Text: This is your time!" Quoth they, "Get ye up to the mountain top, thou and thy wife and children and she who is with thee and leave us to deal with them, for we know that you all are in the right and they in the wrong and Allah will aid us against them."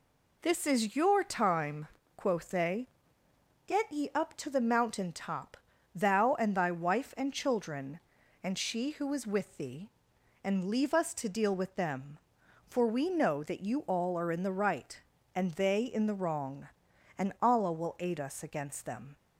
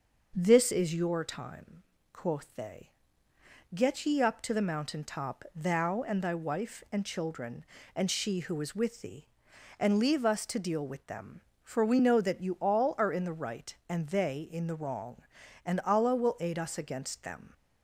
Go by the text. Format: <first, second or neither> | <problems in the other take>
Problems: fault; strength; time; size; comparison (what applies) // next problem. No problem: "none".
neither | none